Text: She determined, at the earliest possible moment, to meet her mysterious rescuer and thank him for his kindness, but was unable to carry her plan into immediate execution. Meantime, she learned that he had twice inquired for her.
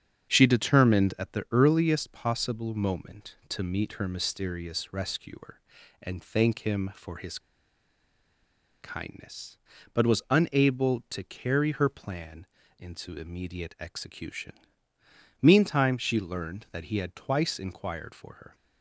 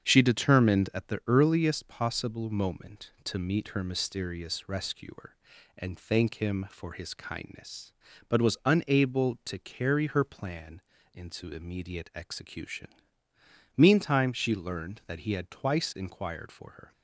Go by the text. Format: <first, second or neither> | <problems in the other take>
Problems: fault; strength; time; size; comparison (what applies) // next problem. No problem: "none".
second | starts louder than the rest; strong; until 1.3 s; 7.5 dB; strong in the second // pauses between "his" and "kindness"; strong; at 7.3 s; 1.4 s long // pauses between "plan" and "into"; slight; at 12.4 s; 0.32 s long; slight in the second